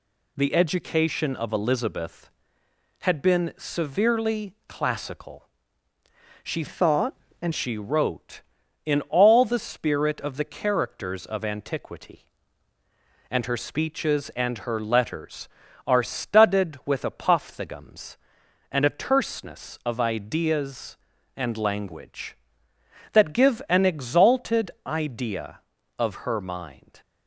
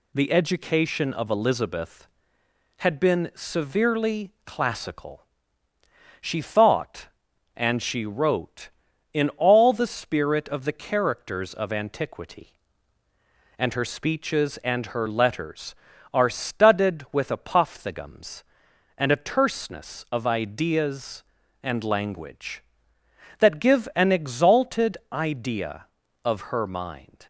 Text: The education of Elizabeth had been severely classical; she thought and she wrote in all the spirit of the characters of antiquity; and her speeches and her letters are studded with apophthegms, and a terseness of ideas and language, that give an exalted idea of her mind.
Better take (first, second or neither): second